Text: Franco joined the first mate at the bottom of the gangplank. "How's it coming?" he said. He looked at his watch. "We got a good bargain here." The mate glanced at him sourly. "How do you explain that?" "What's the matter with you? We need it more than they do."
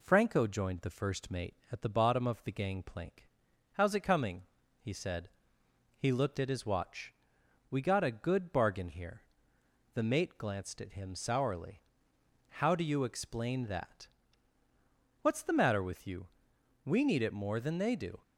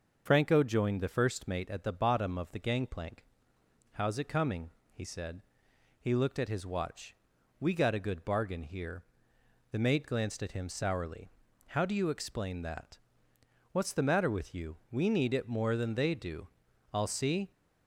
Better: first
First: none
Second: starts louder than the rest; until 1.2 s; 6 dB // goes on to say "I'll see"; from 16.9 s on; 0.58 s long

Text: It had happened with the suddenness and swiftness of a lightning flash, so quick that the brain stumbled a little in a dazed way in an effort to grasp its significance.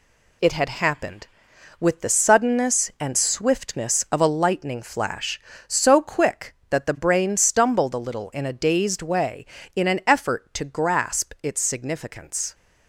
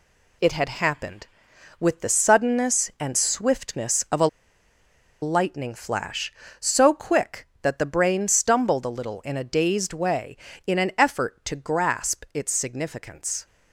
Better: first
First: none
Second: pauses between "a" and "lightning"; noticeable; at 4.2 s; 0.95 s long

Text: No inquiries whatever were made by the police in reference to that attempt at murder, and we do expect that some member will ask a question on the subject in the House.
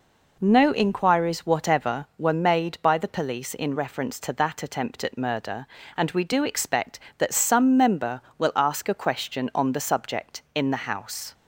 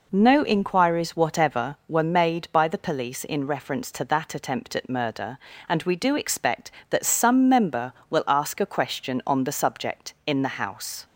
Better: neither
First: none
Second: none

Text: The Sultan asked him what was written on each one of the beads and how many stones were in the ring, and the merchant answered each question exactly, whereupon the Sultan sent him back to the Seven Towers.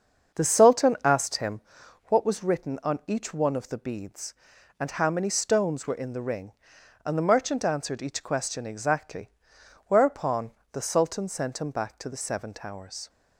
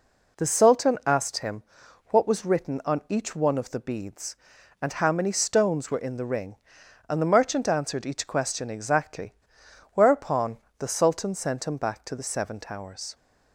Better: second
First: starts louder than the rest; until 2.1 s; 7 dB // pauses between "him" and "what"; noticeable; at 1.6 s; 0.46 s long // pauses between "whereupon" and "the"; slight; at 10.5 s; 0.22 s long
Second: pauses between "him" and "what"; noticeable; at 1.6 s; 0.46 s long // pauses between "whereupon" and "the"; slight; at 10.5 s; 0.22 s long

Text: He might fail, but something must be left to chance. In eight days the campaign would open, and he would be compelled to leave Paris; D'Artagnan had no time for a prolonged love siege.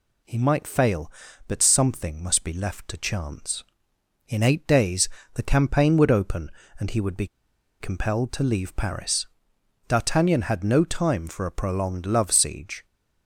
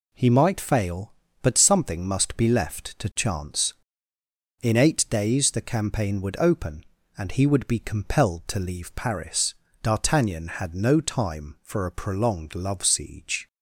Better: second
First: pauses between "days" and "the"; slight; at 5.0 s; 0.24 s long // pauses between "be" and "compelled"; noticeable; at 7.2 s; 0.53 s long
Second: none

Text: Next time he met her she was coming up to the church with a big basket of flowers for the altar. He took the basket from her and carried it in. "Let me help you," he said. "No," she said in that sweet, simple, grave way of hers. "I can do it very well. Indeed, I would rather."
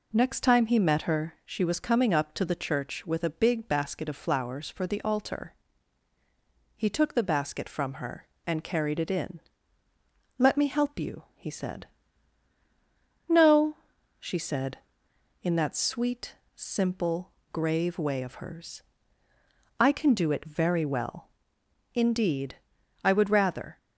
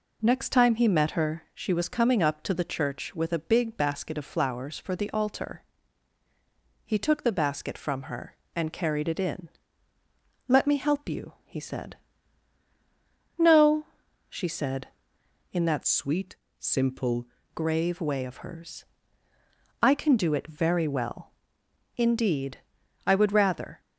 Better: first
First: none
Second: changes voice from "sweet" to "simple"; from 15.8 to 17.2 s; 1.4 s long

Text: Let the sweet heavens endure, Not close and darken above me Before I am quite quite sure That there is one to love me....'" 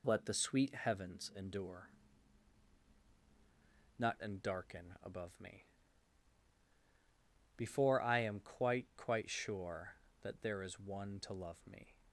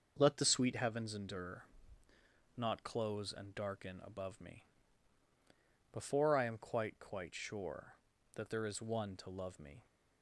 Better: second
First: skips "close"; at 4.2 s // pauses between "me" and "Before"; strong; at 5.6 s; 1.9 s long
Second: pauses between "me" and "Before"; strong; at 4.6 s; 1.3 s long

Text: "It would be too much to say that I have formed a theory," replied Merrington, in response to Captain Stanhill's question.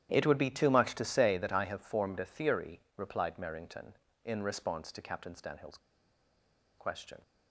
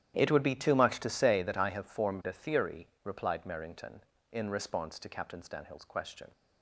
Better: second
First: starts louder than the rest; strong; until 1.1 s; 11.5 dB // pauses between "Stanhill's" and "question"; at 5.7 s; 0.99 s long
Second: starts louder than the rest; strong; until 1.1 s; 11.5 dB

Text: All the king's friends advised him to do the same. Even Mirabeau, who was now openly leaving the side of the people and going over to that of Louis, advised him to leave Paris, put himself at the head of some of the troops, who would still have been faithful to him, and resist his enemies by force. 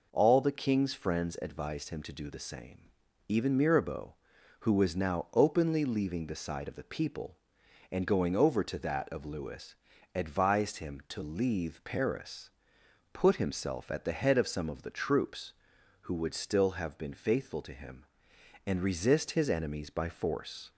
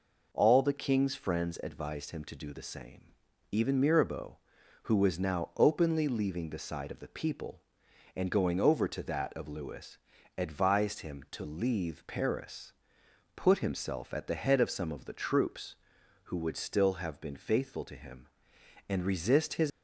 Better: first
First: none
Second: stops before "enemies by force"; at 19.7 s

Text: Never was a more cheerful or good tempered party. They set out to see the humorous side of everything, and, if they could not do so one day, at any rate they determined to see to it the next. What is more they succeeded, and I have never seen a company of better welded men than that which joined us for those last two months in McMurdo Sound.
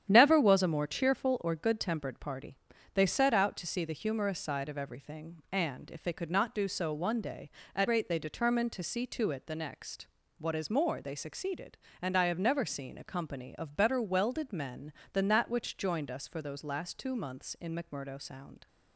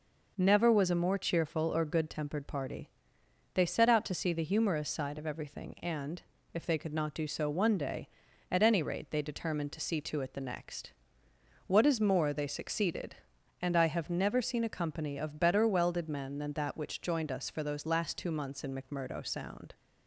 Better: second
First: starts louder than the rest; strong; until 1.1 s; 9.5 dB // skips "any"; at 7.8 s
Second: none

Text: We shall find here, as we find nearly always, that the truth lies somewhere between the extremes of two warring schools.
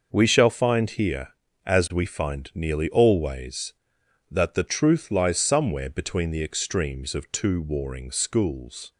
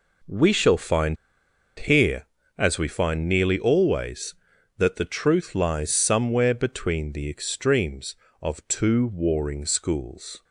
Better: first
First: none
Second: pauses between "find" and "here"; noticeable; at 1.1 s; 0.63 s long

